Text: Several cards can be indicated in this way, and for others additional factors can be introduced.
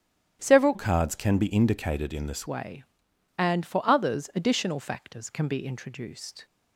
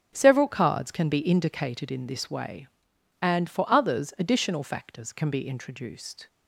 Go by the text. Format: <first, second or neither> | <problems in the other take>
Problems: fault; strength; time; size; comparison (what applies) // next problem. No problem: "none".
second | starts louder than the rest; strong; until 1.4 s; 10 dB; also in the second // changes voice from "cards" to "this"; from 0.7 to 2.4 s; 1.7 s long